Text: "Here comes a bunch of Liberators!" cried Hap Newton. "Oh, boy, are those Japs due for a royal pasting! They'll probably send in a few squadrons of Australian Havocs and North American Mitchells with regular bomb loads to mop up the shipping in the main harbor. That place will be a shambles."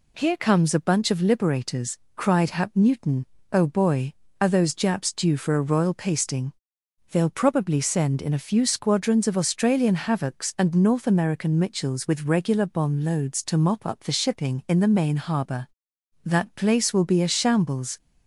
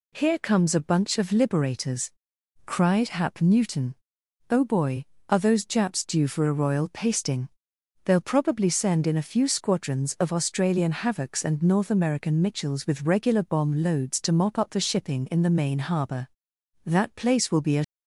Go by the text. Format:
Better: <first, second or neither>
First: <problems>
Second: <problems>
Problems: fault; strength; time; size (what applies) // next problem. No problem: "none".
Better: first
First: none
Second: stops before "shambles"; at 17.8 s